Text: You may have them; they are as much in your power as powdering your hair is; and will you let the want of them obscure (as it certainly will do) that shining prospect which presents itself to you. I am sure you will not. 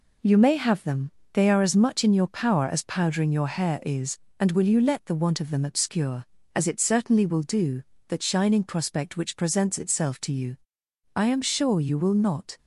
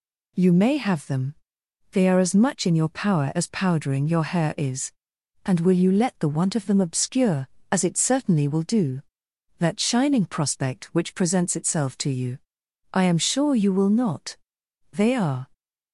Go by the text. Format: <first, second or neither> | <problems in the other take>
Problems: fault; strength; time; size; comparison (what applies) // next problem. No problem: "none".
first | goes on to say "They are"; from 14.9 s on; 0.58 s long